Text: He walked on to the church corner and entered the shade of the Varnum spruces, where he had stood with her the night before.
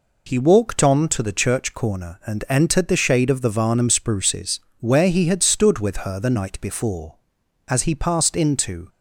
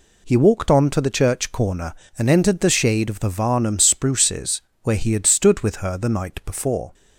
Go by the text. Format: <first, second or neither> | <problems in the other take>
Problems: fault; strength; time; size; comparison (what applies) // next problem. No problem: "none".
second | goes on to say "As he passed into"; noticeable; from 7.6 s on; 1.2 s long